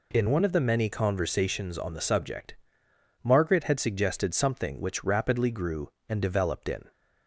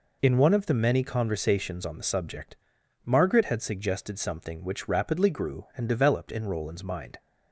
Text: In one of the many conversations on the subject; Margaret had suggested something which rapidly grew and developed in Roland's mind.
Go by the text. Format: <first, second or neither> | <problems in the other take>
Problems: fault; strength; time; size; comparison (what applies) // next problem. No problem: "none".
second | stops before "Roland's mind"; at 6.9 s